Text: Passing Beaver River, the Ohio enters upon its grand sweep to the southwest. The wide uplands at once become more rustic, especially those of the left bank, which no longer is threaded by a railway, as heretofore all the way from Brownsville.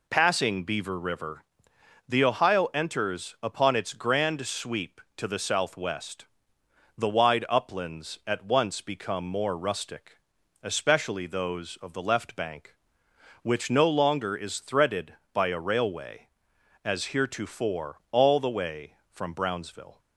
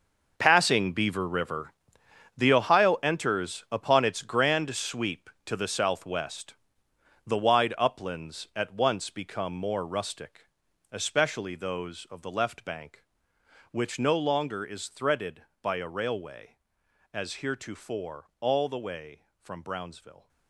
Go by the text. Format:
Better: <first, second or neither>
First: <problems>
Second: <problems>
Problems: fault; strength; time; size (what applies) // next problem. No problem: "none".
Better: first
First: none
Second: gets quieter; strong; throughout; 14 dB